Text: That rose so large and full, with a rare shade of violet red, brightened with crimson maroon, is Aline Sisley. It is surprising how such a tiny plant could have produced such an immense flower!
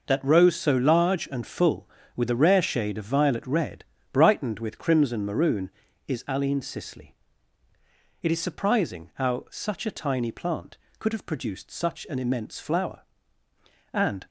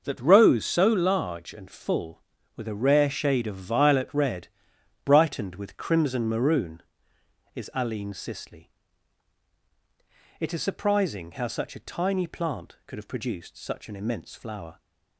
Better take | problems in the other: second | goes on to say "And"; slight; from 13.9 s on; 0.34 s long

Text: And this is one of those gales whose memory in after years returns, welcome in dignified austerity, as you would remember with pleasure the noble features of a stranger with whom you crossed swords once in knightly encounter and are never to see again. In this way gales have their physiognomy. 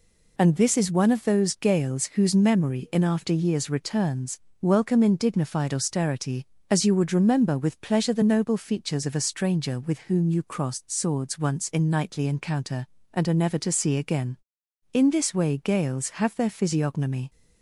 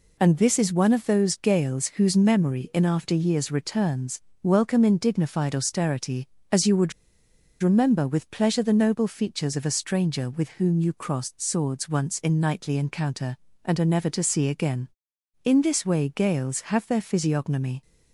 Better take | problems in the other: first | pauses between "would" and "remember"; noticeable; at 6.9 s; 0.70 s long

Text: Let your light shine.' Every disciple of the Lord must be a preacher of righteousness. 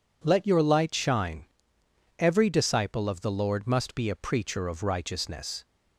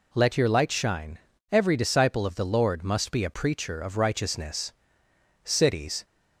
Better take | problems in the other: first | goes on to say "Cities"; from 5.4 s on; 0.60 s long

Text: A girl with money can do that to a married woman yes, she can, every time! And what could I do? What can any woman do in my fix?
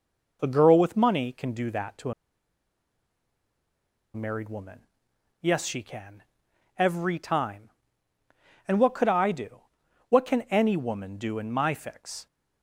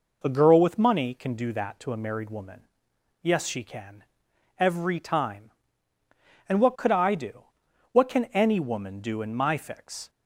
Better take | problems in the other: second | pauses between "to" and "a"; strong; at 2.1 s; 2.0 s long // pauses between "woman" and "yes"; noticeable; at 4.8 s; 0.62 s long; noticeable in the second

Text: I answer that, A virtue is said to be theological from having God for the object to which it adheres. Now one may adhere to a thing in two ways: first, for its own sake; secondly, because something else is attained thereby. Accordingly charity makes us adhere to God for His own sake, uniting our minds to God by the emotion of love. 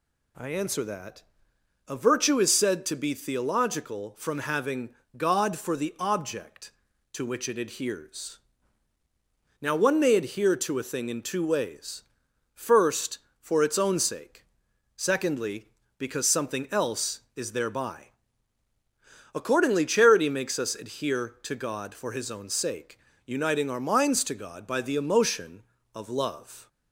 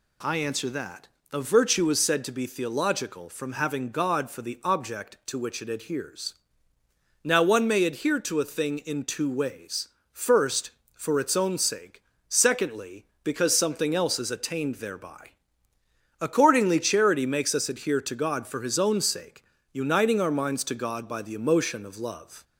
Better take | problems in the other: second | pauses between "having" and "God"; slight; at 4.8 s; 0.26 s long // skips "attained"; at 17.5 s

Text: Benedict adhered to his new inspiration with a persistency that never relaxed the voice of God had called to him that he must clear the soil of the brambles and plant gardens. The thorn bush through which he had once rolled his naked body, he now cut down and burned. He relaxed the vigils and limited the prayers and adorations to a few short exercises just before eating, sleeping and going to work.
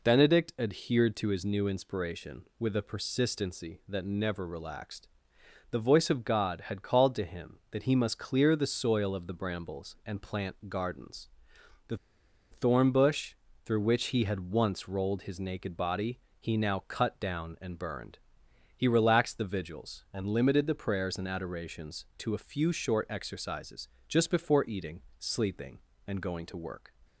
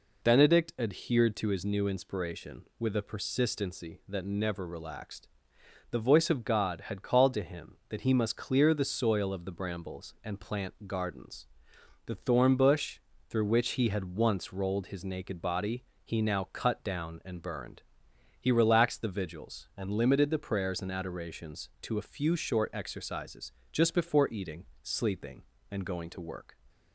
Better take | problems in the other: second | pauses between "relaxed" and "the"; noticeable; at 5.0 s; 0.62 s long; noticeable in the second // pauses between "The" and "thorn"; noticeable; at 11.9 s; 0.56 s long // pauses between "bush" and "through"; slight; at 13.3 s; 0.32 s long; slight in the second // pauses between "exercises" and "just"; slight; at 23.8 s; 0.22 s long; slight in the second

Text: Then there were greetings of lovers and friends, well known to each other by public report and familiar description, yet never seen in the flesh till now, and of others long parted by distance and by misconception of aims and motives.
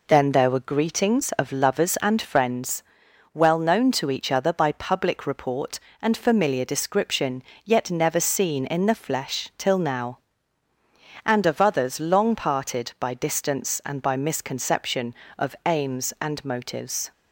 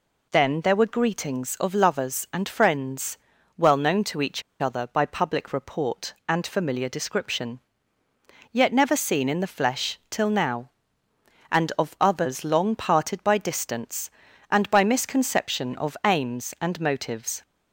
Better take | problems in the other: first | pauses between "each" and "other"; slight; at 4.4 s; 0.19 s long

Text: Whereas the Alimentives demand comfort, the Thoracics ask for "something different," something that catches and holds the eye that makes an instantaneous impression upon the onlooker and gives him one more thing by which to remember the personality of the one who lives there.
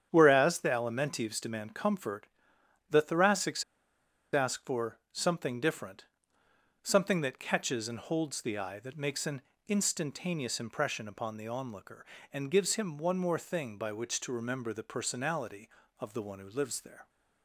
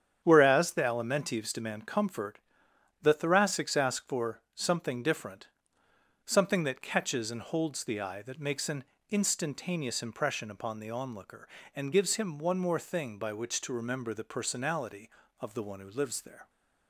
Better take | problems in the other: second | starts louder than the rest; strong; until 1.1 s; 9 dB; strong in the second // pauses between "Thoracics" and "ask"; noticeable; at 3.6 s; 0.69 s long // pauses between "an" and "instantaneous"; slight; at 9.4 s; 0.26 s long; slight in the second

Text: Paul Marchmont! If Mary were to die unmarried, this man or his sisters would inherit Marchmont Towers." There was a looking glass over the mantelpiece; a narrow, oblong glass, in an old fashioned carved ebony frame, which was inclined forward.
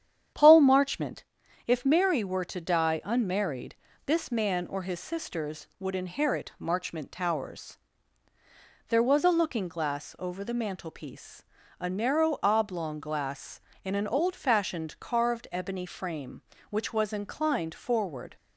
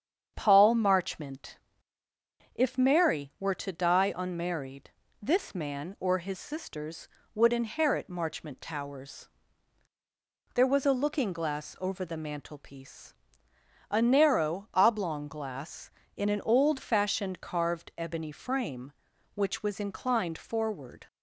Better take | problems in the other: neither | starts louder than the rest; strong; the same in both

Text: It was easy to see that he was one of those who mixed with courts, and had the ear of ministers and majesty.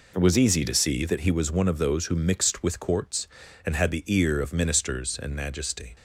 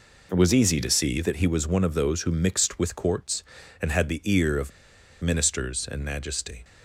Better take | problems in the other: first | pauses between "of" and "ministers"; noticeable; at 4.6 s; 0.52 s long

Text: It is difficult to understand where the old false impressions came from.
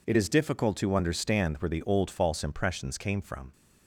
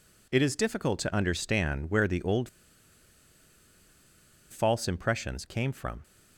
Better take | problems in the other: first | pauses between "old" and "false"; strong; at 2.4 s; 2.0 s long

